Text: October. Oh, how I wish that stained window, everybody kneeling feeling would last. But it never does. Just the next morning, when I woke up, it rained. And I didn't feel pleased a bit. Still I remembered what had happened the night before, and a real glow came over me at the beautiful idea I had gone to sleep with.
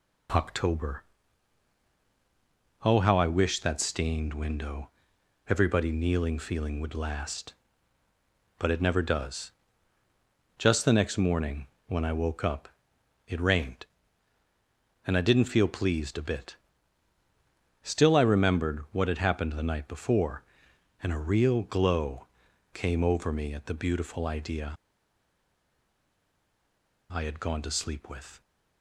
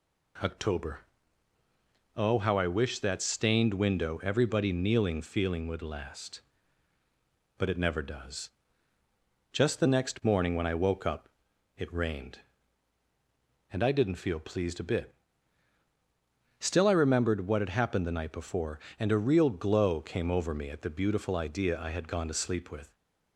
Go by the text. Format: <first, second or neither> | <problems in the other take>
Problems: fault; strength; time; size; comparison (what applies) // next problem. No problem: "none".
second | pauses between "glow" and "came"; noticeable; at 22.2 s; 0.46 s long // pauses between "idea" and "I"; strong; at 24.7 s; 2.3 s long